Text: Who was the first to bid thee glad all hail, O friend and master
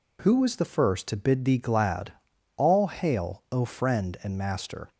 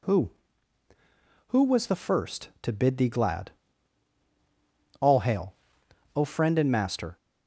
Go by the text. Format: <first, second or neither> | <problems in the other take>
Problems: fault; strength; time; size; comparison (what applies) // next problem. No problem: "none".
first | says "Who" twice; at 1.4 s // pauses between "glad" and "all"; strong; at 3.5 s; 1.4 s long; noticeable in the first